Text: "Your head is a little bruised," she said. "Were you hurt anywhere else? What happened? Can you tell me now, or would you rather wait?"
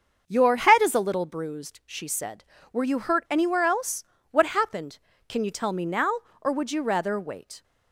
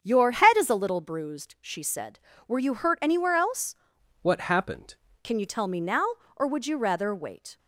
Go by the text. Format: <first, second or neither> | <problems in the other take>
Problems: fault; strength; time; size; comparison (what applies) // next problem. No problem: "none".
first | starts louder than the rest; strong; until 1.0 s; 7.5 dB; also in the first // changes voice from "What" to "happened"; from 4.2 to 4.9 s; 0.7 s long